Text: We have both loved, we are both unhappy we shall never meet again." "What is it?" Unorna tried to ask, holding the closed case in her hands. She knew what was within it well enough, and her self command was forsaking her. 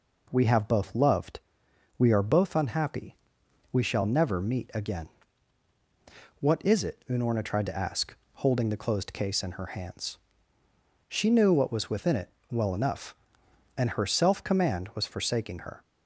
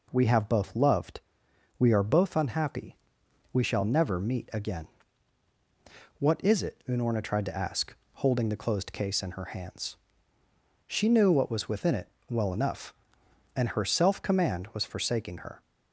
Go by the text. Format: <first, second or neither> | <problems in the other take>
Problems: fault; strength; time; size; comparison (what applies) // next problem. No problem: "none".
neither | pauses between "unhappy" and "we"; noticeable; the same in both // pauses between "it" and "well"; slight; the same in both